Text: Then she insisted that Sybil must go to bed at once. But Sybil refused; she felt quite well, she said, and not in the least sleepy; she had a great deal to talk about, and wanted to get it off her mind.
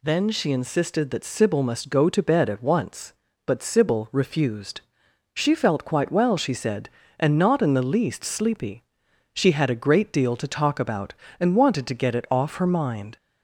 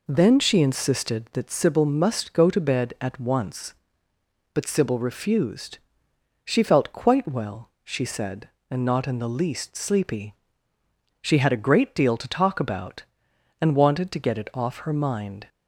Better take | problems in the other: neither | none

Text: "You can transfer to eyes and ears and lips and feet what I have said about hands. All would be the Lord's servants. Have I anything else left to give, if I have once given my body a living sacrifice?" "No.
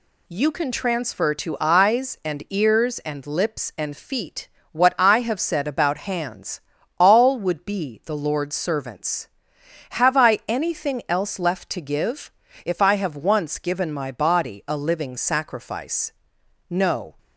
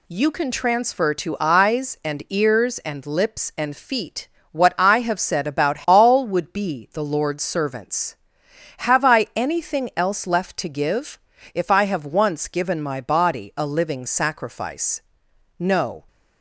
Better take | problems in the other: first | pauses between "feet" and "what"; slight; at 4.2 s; 0.24 s long; slight in the first // skips "hands"; at 5.8 s

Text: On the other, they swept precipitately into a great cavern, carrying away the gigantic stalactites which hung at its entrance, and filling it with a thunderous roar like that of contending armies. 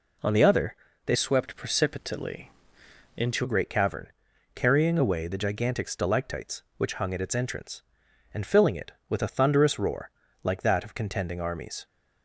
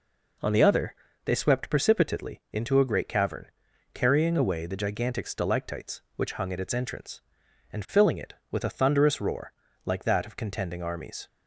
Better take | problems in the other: second | changes voice from "swept" to "into"; from 1.1 to 3.4 s; 2.3 s long // pauses between "precipitately" and "into"; noticeable; at 2.5 s; 0.66 s long // pauses between "roar" and "like"; slight; at 10.1 s; 0.32 s long; slight in the second

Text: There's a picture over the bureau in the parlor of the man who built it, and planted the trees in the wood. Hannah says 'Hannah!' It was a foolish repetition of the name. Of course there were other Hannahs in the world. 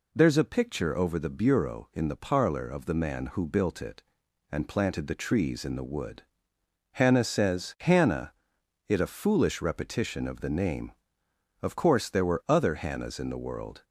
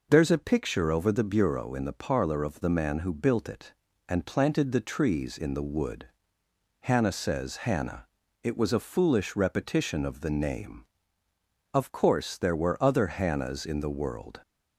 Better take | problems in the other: second | skips "was"; at 8.9 s

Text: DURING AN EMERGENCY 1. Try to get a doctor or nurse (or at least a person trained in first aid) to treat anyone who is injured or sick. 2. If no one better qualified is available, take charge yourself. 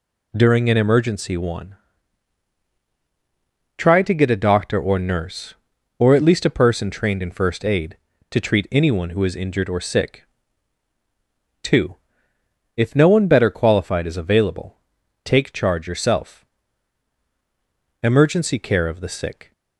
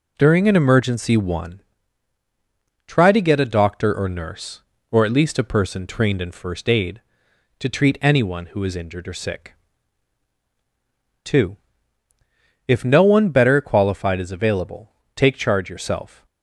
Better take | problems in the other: second | goes on to say "EMERGENCY CARE OF THE SICK"; from 18.0 s on; 1.5 s long

